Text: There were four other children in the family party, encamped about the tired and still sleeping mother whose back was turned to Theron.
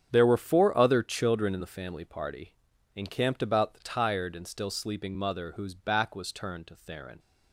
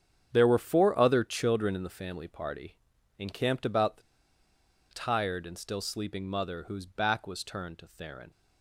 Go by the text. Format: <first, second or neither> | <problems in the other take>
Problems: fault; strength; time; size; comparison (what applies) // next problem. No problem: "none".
first | starts louder than the rest; strong; until 1.3 s; 8 dB; strong in the first // pauses between "the" and "tired"; noticeable; at 4.0 s; 0.88 s long